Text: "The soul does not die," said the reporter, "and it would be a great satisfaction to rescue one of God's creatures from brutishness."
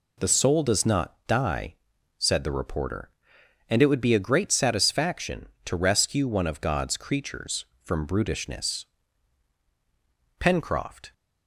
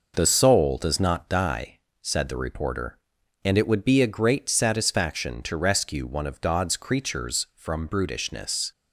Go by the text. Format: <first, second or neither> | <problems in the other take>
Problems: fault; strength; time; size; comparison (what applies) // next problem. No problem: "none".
second | goes on to say "Pencroft"; noticeable; from 10.4 s on; 0.72 s long